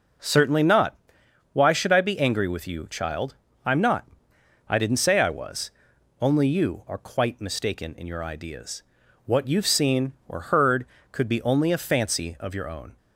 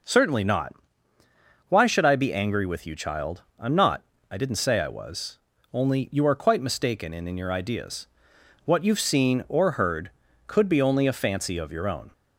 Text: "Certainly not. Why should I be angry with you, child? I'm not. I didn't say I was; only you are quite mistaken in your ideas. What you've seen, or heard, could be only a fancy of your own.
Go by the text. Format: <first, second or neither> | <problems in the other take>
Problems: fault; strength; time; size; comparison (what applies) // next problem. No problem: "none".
first | says "in" twice; at 7.2 s